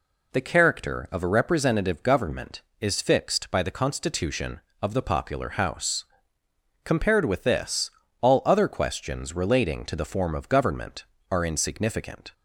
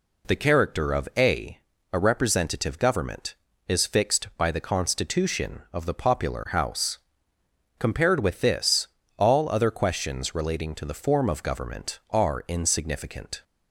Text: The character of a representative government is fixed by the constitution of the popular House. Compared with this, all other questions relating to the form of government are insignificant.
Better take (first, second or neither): first